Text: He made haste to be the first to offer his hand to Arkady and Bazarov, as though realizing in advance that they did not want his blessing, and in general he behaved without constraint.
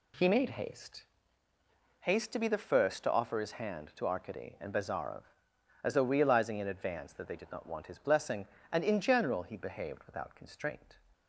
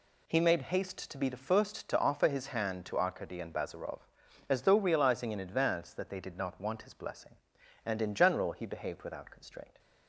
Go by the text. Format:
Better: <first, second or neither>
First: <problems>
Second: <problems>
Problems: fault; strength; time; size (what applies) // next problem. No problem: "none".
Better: second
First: says "haste" twice; at 2.0 s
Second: none